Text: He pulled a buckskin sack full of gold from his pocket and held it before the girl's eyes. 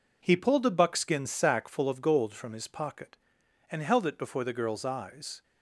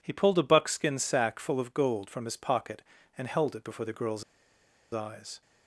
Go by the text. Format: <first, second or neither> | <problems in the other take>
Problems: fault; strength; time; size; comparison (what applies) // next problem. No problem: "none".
first | pauses between "girl's" and "eyes"; noticeable; at 4.2 s; 0.69 s long